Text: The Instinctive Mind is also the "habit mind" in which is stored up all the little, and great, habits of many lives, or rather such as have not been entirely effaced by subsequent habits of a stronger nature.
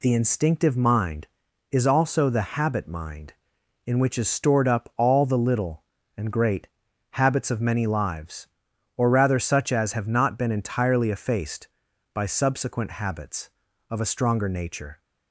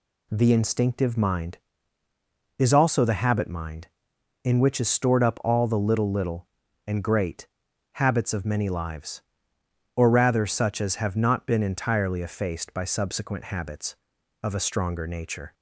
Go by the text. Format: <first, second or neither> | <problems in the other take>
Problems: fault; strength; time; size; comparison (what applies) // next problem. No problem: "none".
first | says "little" twice; at 6.1 s